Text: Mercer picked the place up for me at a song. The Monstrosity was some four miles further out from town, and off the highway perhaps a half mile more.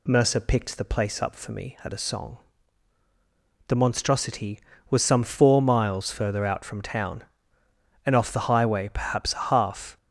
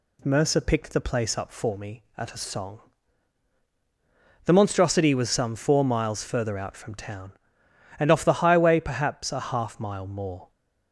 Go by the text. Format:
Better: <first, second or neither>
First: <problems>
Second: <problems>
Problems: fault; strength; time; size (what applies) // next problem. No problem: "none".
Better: second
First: stops before "mile more"; at 9.9 s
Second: none